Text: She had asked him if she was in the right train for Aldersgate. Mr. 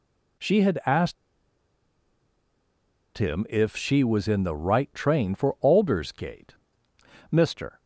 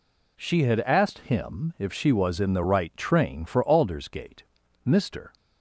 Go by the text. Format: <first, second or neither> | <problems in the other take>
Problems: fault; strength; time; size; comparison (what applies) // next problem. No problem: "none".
second | pauses between "asked" and "him"; strong; at 1.1 s; 2.0 s long